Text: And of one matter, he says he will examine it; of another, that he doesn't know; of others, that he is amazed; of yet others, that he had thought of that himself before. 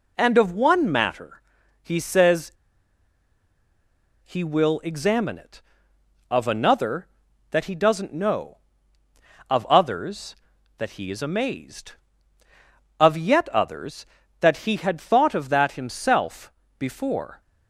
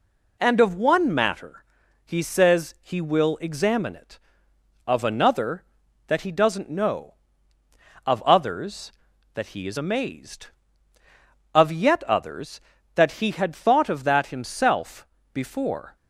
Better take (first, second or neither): second